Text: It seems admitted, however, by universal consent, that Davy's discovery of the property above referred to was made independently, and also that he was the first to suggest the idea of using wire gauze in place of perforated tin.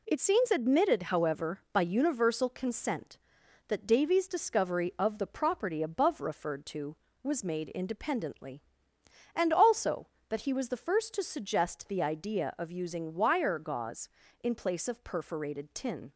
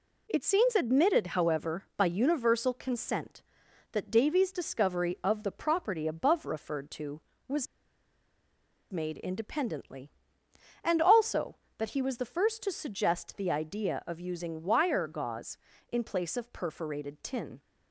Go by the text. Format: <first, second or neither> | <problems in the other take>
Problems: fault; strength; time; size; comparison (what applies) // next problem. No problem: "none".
first | pauses between "was" and "made"; strong; at 7.6 s; 1.2 s long